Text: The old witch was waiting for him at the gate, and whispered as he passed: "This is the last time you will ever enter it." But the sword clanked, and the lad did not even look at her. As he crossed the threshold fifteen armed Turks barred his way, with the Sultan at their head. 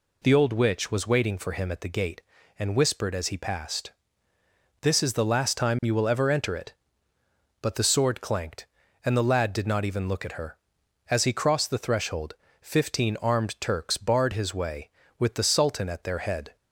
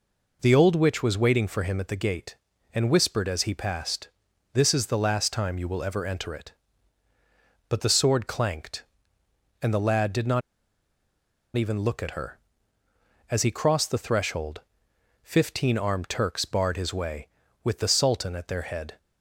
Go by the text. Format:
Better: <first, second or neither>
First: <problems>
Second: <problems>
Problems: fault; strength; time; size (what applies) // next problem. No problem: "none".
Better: first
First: pauses between "threshold" and "fifteen"; slight; at 12.3 s; 0.26 s long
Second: pauses between "not" and "even"; at 10.4 s; 1.1 s long // pauses between "threshold" and "fifteen"; noticeable; at 14.6 s; 0.60 s long